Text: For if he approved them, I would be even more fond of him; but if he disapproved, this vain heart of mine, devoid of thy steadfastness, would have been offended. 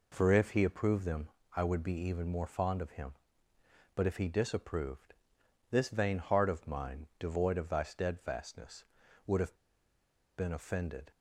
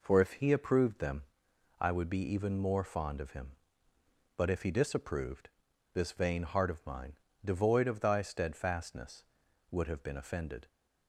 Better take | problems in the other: second | pauses between "have" and "been"; noticeable; at 9.5 s; 0.82 s long

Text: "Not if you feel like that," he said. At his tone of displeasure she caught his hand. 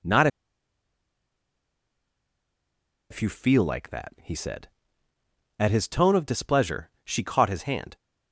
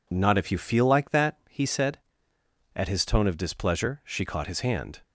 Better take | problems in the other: second | pauses between "Not" and "if"; strong; at 0.2 s; 2.8 s long

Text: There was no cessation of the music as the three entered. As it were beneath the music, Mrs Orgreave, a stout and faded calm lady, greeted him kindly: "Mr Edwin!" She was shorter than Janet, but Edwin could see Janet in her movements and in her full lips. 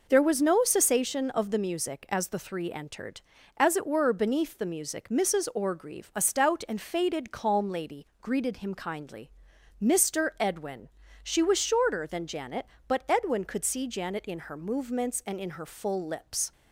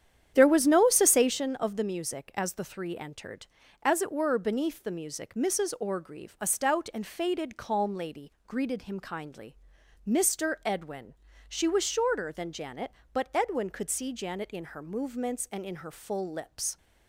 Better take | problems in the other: first | starts louder than the rest; strong; until 1.5 s; 9.5 dB

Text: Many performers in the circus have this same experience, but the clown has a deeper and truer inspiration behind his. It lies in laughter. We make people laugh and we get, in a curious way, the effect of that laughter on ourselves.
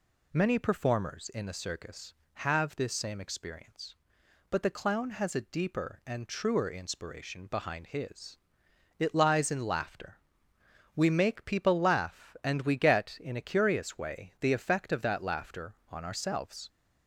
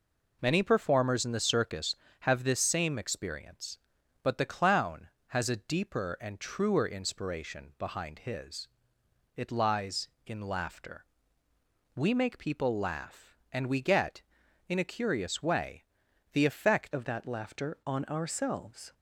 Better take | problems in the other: first | changes voice at "of"; from 16.9 s on; 2.0 s long

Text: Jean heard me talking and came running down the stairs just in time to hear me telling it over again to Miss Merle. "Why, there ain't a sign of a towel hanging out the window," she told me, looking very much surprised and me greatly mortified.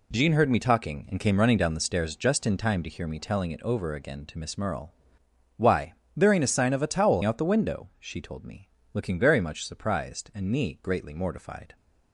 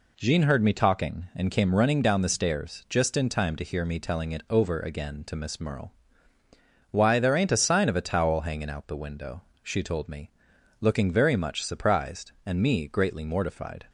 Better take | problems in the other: second | skips "hanging"; at 7.2 s

